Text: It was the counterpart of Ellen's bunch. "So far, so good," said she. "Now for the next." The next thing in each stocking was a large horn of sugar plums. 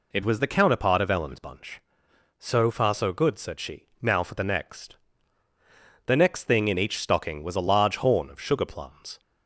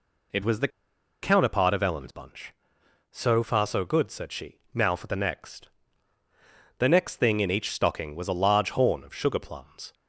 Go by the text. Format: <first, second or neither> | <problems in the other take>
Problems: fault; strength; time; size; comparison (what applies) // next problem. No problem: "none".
first | pauses between "the" and "counterpart"; noticeable; at 0.6 s; 0.54 s long